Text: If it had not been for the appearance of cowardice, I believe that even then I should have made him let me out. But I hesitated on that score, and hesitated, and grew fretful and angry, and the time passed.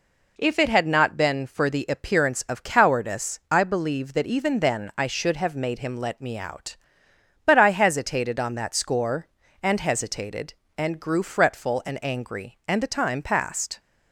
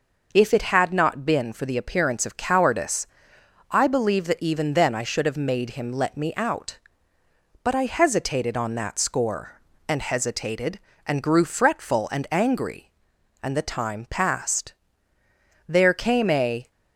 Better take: first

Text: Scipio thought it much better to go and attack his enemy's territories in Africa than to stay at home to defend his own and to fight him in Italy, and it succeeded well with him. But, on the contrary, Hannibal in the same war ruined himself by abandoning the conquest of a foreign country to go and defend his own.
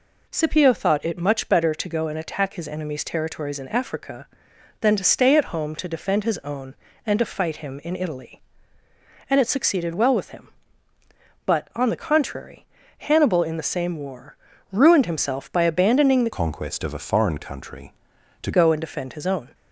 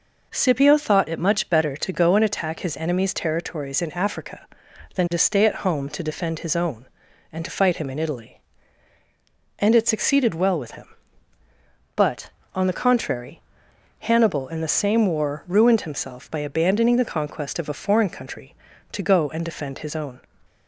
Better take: second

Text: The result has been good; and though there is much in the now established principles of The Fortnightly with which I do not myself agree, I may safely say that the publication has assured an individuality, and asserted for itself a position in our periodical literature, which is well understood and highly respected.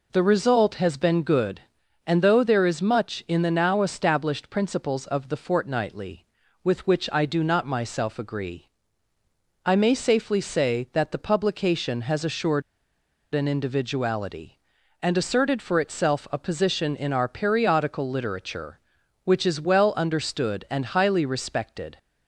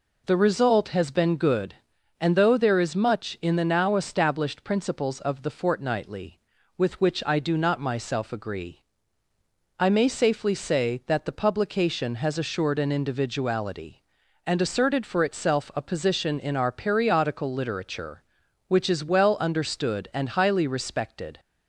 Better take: second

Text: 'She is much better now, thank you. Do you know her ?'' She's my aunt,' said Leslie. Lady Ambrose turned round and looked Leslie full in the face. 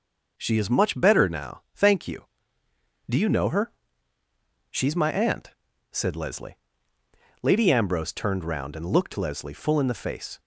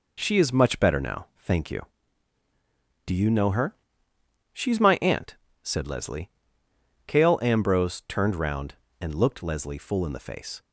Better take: first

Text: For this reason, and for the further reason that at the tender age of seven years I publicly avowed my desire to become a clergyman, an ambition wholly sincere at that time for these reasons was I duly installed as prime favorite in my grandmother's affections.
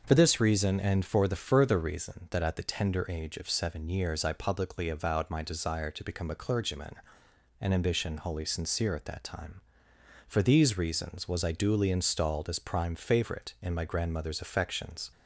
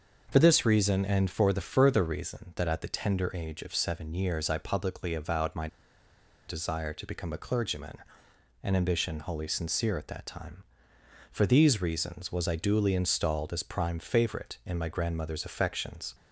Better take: first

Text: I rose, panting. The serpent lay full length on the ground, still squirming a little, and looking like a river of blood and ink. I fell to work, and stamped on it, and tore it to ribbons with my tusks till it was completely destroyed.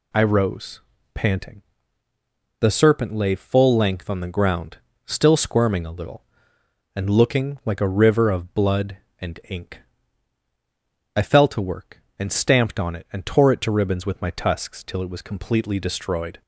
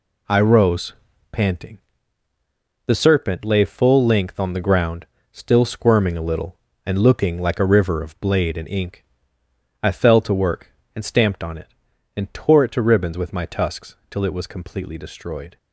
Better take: first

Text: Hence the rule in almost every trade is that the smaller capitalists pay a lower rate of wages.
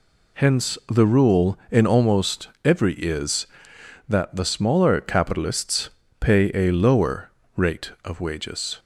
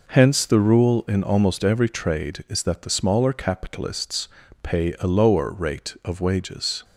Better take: second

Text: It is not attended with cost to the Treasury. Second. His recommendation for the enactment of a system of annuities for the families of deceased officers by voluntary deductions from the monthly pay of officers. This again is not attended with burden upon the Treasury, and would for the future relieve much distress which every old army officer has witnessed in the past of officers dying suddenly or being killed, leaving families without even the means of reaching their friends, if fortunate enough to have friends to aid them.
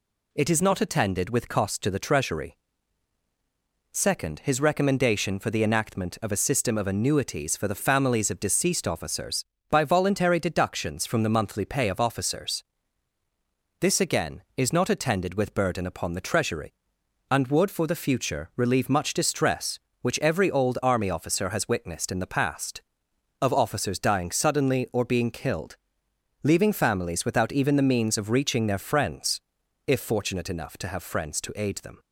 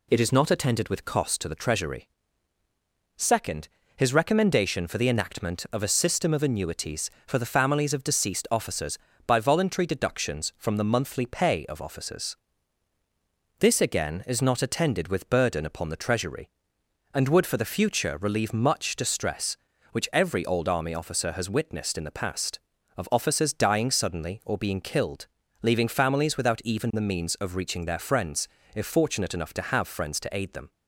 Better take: neither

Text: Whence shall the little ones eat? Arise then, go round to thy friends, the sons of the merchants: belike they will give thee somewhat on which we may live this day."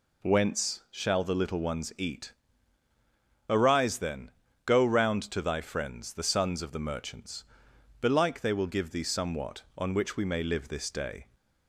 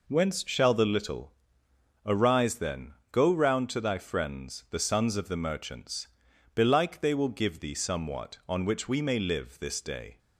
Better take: first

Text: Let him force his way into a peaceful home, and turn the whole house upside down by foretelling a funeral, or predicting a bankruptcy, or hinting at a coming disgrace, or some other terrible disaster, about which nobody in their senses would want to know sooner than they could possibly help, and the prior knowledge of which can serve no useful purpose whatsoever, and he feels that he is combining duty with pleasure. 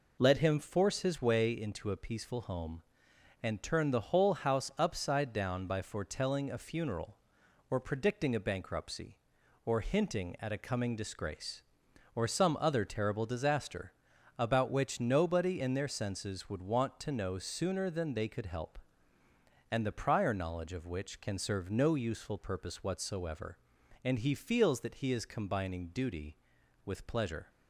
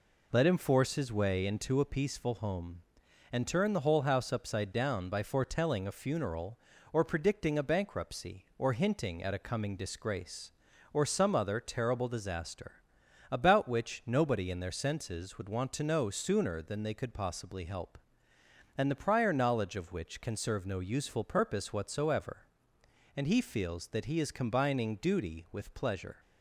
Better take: second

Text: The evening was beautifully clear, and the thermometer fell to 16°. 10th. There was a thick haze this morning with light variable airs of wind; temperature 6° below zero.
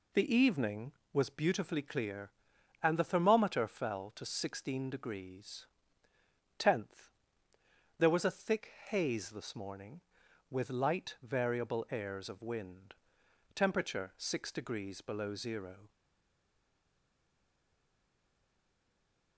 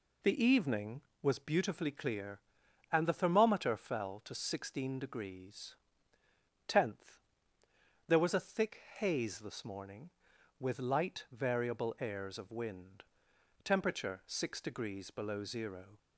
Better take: second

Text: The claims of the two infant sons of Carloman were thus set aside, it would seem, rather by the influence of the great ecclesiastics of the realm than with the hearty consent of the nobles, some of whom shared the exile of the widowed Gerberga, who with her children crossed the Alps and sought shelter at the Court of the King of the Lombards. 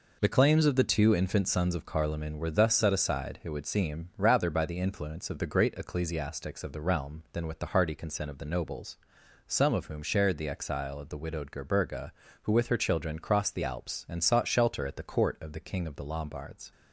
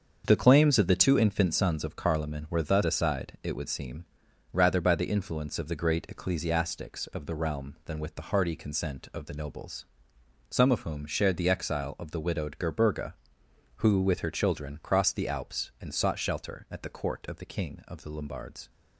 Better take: first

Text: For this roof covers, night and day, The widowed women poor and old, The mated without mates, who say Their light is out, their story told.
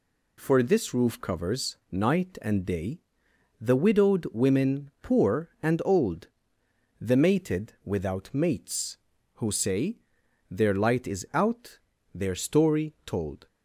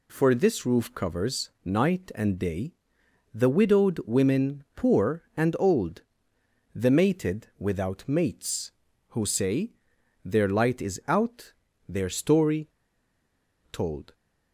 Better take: first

